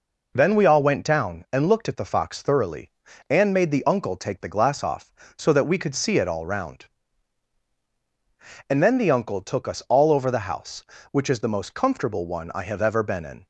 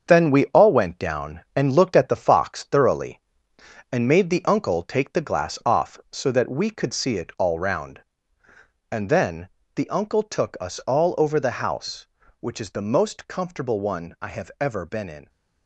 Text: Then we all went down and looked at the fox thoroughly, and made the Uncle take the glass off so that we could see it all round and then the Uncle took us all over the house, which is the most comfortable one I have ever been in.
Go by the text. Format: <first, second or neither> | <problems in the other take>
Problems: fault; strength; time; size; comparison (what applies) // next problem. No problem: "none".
first | gets quieter; throughout; 7 dB // pauses between "then" and "the"; slight; at 9.4 s; 0.30 s long